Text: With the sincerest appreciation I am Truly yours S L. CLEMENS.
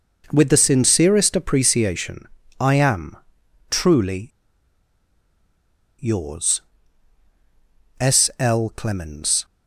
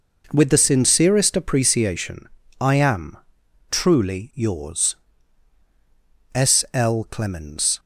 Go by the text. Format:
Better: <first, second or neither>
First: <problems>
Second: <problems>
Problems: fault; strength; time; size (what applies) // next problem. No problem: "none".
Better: second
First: pauses between "appreciation" and "I"; slight; at 2.2 s; 0.32 s long // pauses between "am" and "Truly"; noticeable; at 3.1 s; 0.52 s long // pauses between "Truly" and "yours"; strong; at 4.2 s; 1.7 s long // pauses between "yours" and "S"; strong; at 6.6 s; 1.3 s long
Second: pauses between "appreciation" and "I"; slight; at 2.2 s; 0.32 s long // pauses between "am" and "Truly"; noticeable; at 3.1 s; 0.52 s long // pauses between "yours" and "S"; strong; at 4.9 s; 1.3 s long